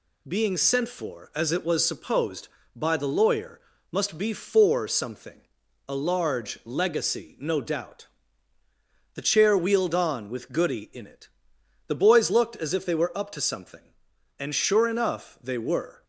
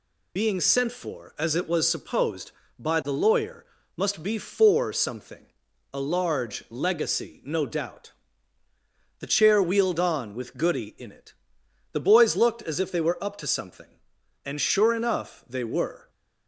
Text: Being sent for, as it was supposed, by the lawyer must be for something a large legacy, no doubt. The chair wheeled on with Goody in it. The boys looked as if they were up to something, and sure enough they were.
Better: first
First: pauses between "lawyer" and "must"; slight; at 3.5 s; 0.32 s long // pauses between "something" and "a"; noticeable; at 5.4 s; 0.48 s long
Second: loses the start of "Being"; at 0.3 s; 65 ms // pauses between "lawyer" and "must"; slight; at 3.6 s; 0.32 s long // pauses between "something" and "a"; noticeable; at 5.4 s; 0.48 s long

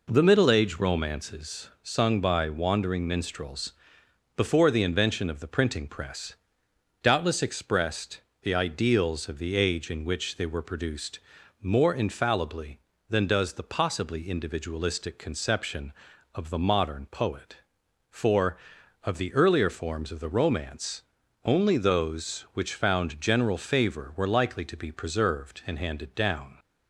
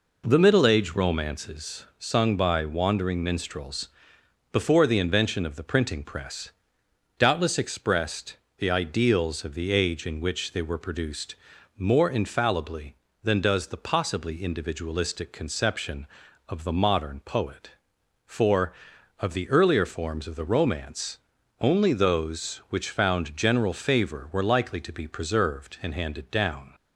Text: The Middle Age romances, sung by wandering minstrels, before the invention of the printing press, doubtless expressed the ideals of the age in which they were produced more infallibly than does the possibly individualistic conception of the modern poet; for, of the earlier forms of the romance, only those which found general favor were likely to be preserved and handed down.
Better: neither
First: pauses between "expressed" and "the"; slight; at 8.2 s; 0.18 s long // pauses between "produced" and "more"; at 11.1 s; 0.42 s long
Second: pauses between "expressed" and "the"; slight; at 8.3 s; 0.18 s long // pauses between "produced" and "more"; at 11.3 s; 0.42 s long

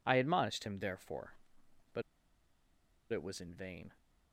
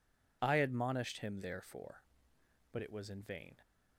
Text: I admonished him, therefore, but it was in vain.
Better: second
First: pauses between "but" and "it"; at 2.0 s; 1.1 s long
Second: none

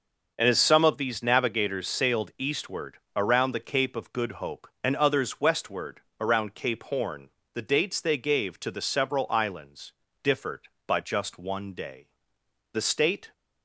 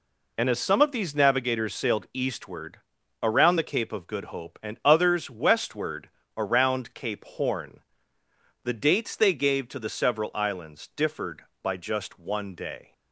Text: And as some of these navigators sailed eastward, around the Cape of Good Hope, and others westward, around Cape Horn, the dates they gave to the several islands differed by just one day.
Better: second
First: pauses between "islands" and "differed"; slight; at 9.9 s; 0.32 s long // goes on to say "The state"; from 12.7 s on; 0.60 s long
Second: none

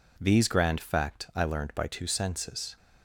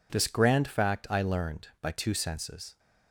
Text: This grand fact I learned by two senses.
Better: second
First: says "These" for "This"; at 0.1 s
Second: none

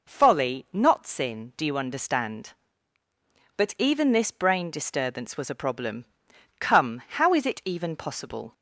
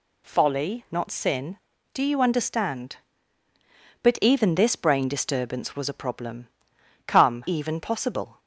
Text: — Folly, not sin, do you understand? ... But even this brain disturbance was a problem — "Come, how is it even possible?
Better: first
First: none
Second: skips "how is it"; at 7.4 s

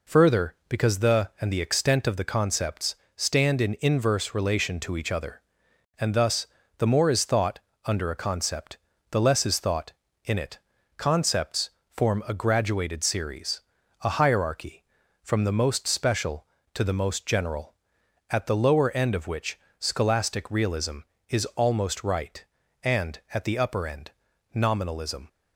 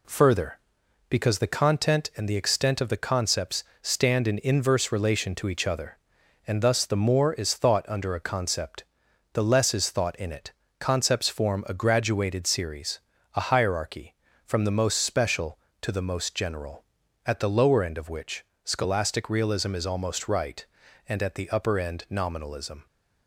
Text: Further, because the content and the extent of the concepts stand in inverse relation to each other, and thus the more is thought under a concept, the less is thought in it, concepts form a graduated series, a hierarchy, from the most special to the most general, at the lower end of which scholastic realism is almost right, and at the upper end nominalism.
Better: second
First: skips "content"; at 1.3 s // pauses between "concepts" and "stand"; slight; at 2.9 s; 0.22 s long // pauses between "thus" and "the"; slight; at 6.4 s; 0.32 s long // pauses between "thought" and "under"; slight; at 7.5 s; 0.24 s long // pauses between "concepts" and "form"; slight; at 11.6 s; 0.22 s long // pauses between "which" and "scholastic"; slight; at 19.5 s; 0.18 s long // pauses between "end" and "nominalism"; at 24.1 s; 0.42 s long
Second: pauses between "concepts" and "stand"; slight; at 3.6 s; 0.18 s long // pauses between "which" and "scholastic"; slight; at 18.4 s; 0.20 s long

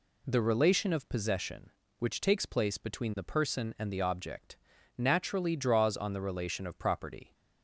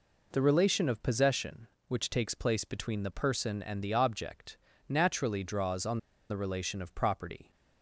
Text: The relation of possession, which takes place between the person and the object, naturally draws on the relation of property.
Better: first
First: none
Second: pauses between "on" and "the"; slight; at 5.9 s; 0.32 s long

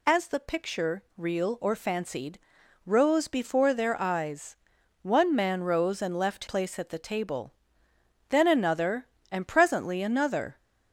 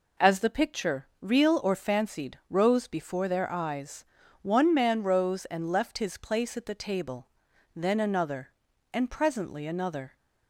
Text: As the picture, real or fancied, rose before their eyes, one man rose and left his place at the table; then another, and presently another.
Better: second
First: skips "his"; at 6.4 s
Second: none

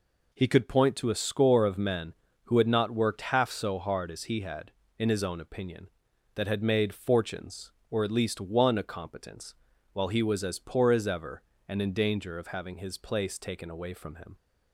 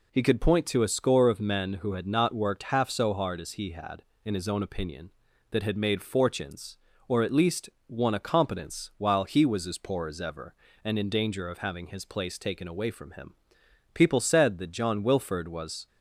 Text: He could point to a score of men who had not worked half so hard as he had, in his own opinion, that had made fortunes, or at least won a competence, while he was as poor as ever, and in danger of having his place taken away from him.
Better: first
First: none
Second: pauses between "least" and "won"; slight; at 7.6 s; 0.18 s long // goes on to say "People said that John Wilford was"; strong; from 13.9 s on; 1.9 s long

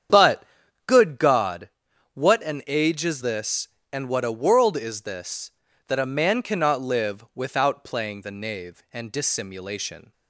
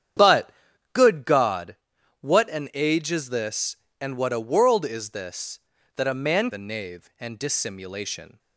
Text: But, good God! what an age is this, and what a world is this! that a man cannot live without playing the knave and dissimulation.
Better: first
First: starts louder than the rest; strong; until 1.5 s; 8.5 dB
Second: starts louder than the rest; strong; until 1.6 s; 9 dB // skips "cannot live without playing"; at 6.5 s

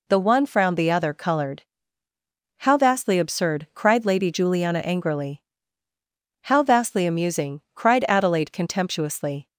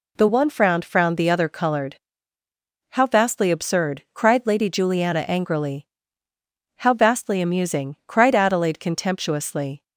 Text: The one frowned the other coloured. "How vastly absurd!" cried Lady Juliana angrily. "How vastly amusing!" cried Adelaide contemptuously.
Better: first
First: none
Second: says "frowned" twice; at 0.8 s

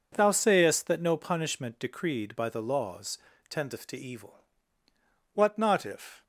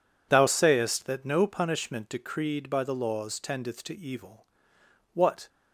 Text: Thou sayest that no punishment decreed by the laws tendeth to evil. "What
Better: second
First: pauses between "laws" and "tendeth"; slight; at 3.1 s; 0.32 s long // goes on to say "not if"; noticeable; from 5.5 s on; 0.64 s long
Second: none

